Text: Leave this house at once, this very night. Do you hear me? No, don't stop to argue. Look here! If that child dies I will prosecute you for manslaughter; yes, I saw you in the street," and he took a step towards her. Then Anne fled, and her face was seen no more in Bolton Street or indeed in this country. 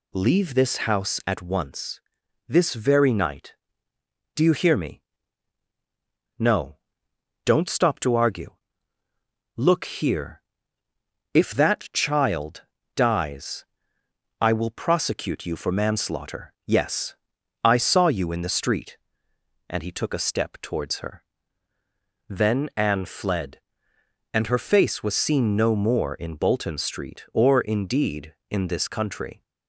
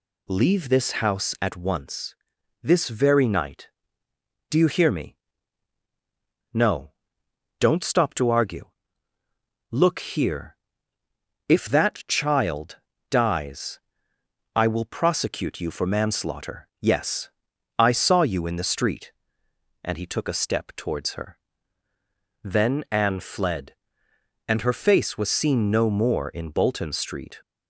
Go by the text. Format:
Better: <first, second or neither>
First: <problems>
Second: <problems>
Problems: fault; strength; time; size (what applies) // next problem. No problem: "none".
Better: first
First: pauses between "child" and "dies"; slight; at 12.6 s; 0.34 s long // pauses between "dies" and "I"; noticeable; at 13.6 s; 0.74 s long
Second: pauses between "child" and "dies"; slight; at 12.7 s; 0.34 s long // pauses between "dies" and "I"; noticeable; at 13.7 s; 0.74 s long // stops before "or indeed in this country"; at 27.4 s